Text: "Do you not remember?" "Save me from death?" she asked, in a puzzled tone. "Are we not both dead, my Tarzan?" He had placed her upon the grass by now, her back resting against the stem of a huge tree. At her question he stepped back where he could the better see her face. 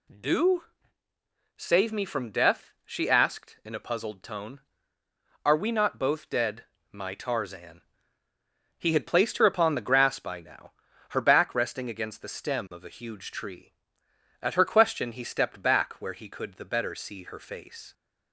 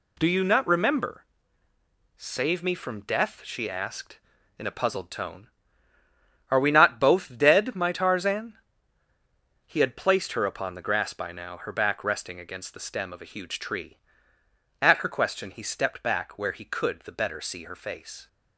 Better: second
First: skips "you not remember"; at 1.1 s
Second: none

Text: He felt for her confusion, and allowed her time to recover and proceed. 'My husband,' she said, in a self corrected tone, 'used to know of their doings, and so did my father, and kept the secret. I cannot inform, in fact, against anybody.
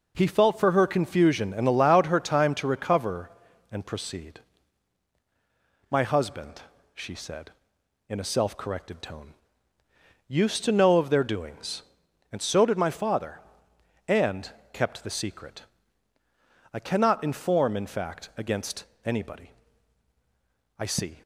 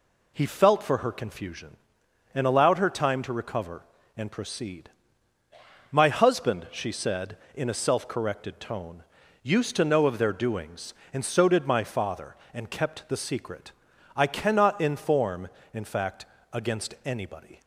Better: second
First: pauses between "and" and "kept"; slight; at 14.5 s; 0.20 s long // pauses between "against" and "anybody"; slight; at 18.8 s; 0.18 s long // goes on to say "I see"; slight; from 20.7 s on; 0.42 s long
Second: none

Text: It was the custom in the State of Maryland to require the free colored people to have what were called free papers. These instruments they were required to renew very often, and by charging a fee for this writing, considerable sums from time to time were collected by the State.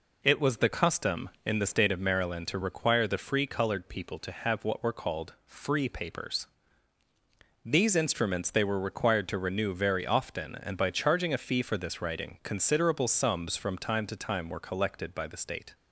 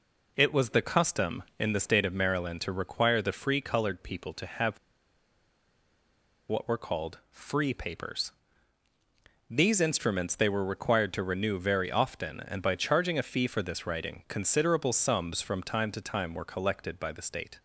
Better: first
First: none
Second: pauses between "have" and "what"; strong; at 4.7 s; 1.7 s long

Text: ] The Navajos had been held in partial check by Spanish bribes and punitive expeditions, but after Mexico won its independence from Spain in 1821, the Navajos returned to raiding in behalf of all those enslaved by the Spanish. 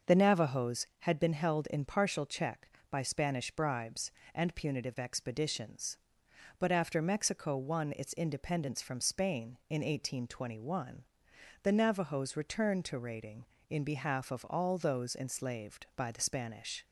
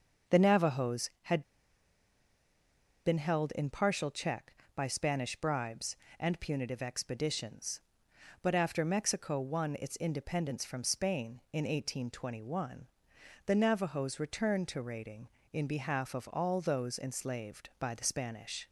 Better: first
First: starts louder than the rest; noticeable; until 1.2 s; 6 dB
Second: starts louder than the rest; noticeable; until 3.0 s; 6 dB // pauses between "had" and "been"; strong; at 1.4 s; 1.6 s long

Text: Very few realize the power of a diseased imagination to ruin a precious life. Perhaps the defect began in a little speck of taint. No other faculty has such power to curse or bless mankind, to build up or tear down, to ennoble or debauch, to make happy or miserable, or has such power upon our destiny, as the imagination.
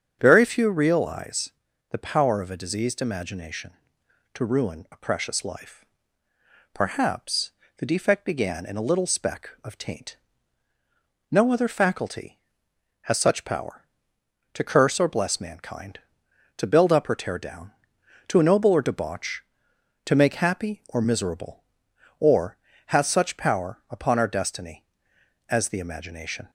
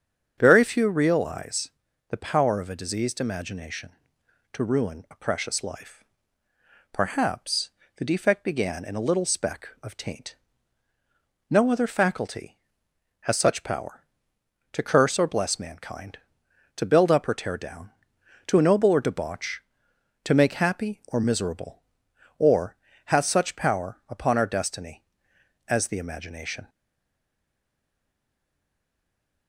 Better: first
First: starts louder than the rest; strong; until 1.2 s; 7.5 dB // pauses between "realize" and "the"; at 1.4 s; 0.42 s long // pauses between "Perhaps" and "the"; slight; at 7.5 s; 0.26 s long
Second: starts louder than the rest; strong; until 1.3 s; 7.5 dB // pauses between "realize" and "the"; at 1.6 s; 0.42 s long // pauses between "Perhaps" and "the"; slight; at 7.7 s; 0.26 s long // stays silent after the last word; strong; from 26.6 s on; 2.8 s long

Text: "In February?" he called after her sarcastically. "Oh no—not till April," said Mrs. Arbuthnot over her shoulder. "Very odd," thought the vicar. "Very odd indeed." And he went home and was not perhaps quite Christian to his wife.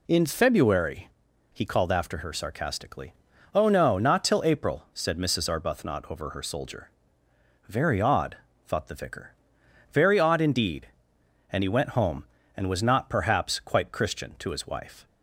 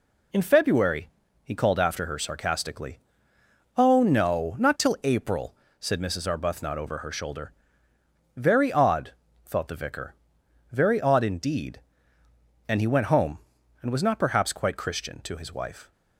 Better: second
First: says "soldier" for "shoulder"; at 6.4 s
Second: none

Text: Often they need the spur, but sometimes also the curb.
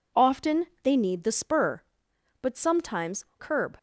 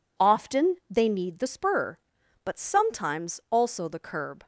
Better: second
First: pauses between "Often" and "they"; slight; at 0.6 s; 0.18 s long // skips "also the"; at 3.3 s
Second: none

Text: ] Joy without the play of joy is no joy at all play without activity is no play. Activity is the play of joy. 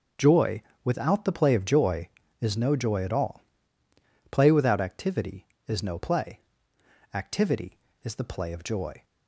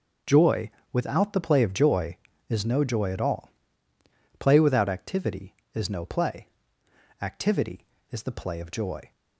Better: neither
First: pauses between "Joy" and "without"; slight; at 0.6 s; 0.22 s long // pauses between "all" and "play"; noticeable; at 3.4 s; 0.88 s long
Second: pauses between "Joy" and "without"; slight; at 0.7 s; 0.22 s long // pauses between "all" and "play"; noticeable; at 3.5 s; 0.88 s long

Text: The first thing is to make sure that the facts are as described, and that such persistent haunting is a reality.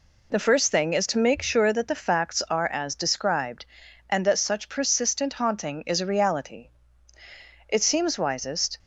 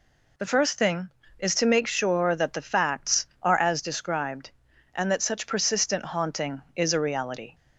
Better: second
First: goes on to say "It seems wisest"; noticeable; from 7.6 s on; 1.1 s long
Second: none

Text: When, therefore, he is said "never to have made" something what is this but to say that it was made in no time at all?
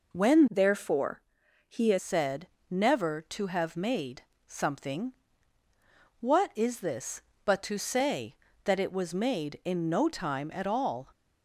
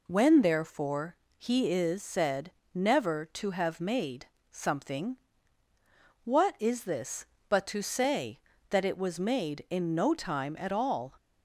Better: second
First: changes voice from "therefore" to "is"; from 0.5 to 1.9 s; 1.4 s long // pauses between "said" and "never"; slight; at 2.4 s; 0.24 s long // pauses between "made" and "something"; slight; at 4.2 s; 0.24 s long // pauses between "something" and "what"; at 5.1 s; 1.0 s long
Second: pauses between "said" and "never"; slight; at 2.5 s; 0.24 s long // pauses between "made" and "something"; slight; at 4.2 s; 0.24 s long // pauses between "something" and "what"; at 5.1 s; 1.0 s long

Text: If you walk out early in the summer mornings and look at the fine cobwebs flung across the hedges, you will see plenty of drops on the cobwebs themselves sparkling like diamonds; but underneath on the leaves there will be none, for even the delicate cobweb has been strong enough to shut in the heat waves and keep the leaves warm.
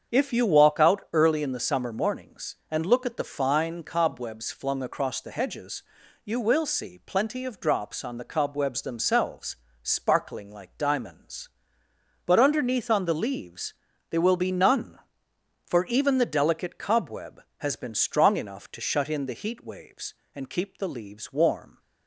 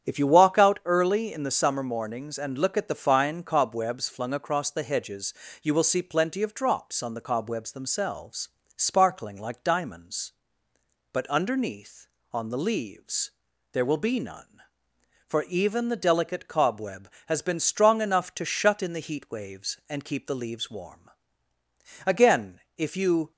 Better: first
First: starts louder than the rest; strong; until 1.1 s; 7 dB // pauses between "themselves" and "sparkling"; slight; at 9.5 s; 0.26 s long // pauses between "leaves" and "there"; at 13.7 s; 0.38 s long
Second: starts louder than the rest; strong; until 1.1 s; 8.5 dB // pauses between "themselves" and "sparkling"; slight; at 8.4 s; 0.28 s long // pauses between "leaves" and "there"; at 13.3 s; 0.40 s long // goes on to say "Again if you"; noticeable; from 22.0 s on; 1.2 s long

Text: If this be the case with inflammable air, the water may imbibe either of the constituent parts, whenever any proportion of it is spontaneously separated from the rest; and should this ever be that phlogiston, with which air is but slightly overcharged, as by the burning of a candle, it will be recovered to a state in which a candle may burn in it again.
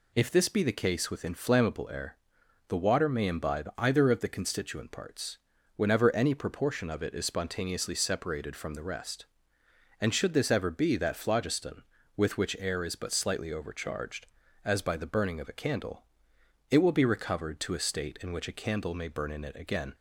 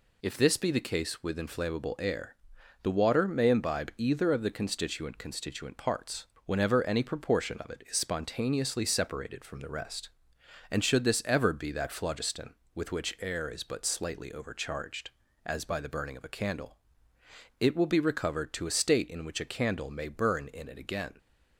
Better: first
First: none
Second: says "constituent" twice; at 5.1 s

